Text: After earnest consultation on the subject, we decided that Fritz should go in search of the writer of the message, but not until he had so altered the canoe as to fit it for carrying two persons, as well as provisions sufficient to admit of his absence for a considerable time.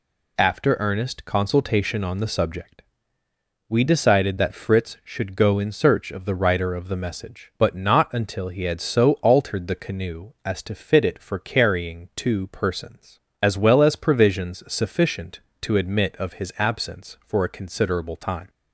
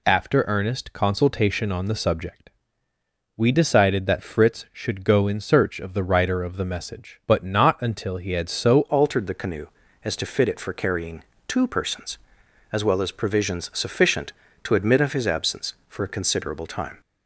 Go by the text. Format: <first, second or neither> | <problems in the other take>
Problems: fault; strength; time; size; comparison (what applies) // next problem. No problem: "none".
first | changes voice at "altered"; from 8.8 s on; 8.2 s long // pauses between "carrying" and "two"; slight; at 11.2 s; 0.24 s long